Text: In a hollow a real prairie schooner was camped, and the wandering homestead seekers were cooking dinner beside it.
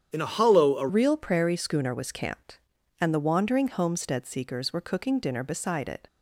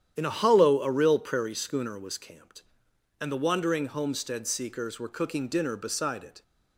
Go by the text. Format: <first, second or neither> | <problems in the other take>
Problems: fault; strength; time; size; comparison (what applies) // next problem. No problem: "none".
second | starts louder than the rest; strong; until 1.1 s; 9 dB; strong in the second // changes voice at "real"; from 0.8 s on; 5.2 s long